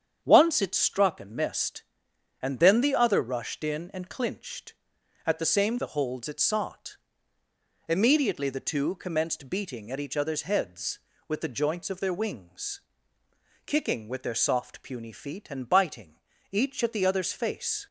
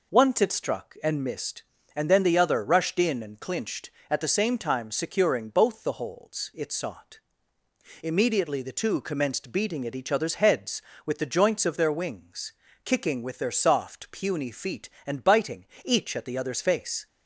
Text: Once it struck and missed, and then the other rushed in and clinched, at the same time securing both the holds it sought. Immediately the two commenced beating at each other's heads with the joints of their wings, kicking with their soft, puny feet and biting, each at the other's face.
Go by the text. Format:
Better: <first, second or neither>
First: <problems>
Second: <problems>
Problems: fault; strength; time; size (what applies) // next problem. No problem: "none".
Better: second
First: starts louder than the rest; strong; until 1.2 s; 8 dB // skips "time securing both"; at 5.7 s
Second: none